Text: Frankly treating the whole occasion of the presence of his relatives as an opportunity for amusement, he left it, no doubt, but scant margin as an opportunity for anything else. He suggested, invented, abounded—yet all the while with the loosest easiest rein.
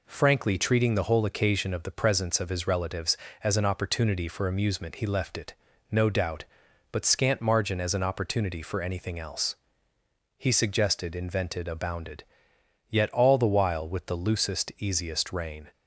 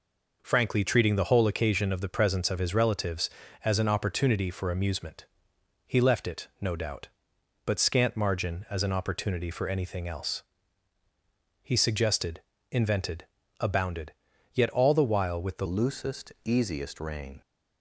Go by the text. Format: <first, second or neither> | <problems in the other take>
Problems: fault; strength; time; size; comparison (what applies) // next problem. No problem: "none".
first | changes voice at "loosest"; from 15.6 s on; 1.8 s long